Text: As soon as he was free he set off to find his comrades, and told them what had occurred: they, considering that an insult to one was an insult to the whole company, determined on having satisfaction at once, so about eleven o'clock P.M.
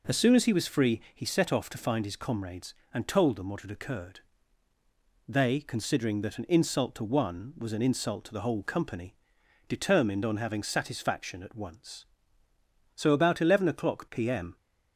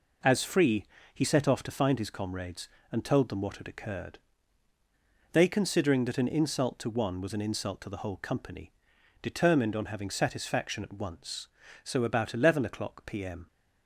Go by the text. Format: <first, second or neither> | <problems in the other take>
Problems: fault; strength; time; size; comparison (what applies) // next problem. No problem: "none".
first | skips "soon as he was"; at 0.4 s // pauses between "free" and "he"; slight; at 0.8 s; 0.28 s long